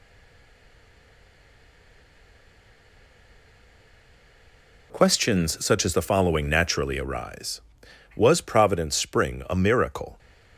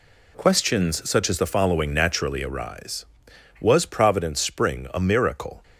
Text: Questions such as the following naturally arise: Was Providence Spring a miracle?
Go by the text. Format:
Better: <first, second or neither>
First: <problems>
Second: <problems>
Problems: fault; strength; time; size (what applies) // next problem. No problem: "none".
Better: second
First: stays silent before the first word; strong; until 4.9 s; 4.9 s long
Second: none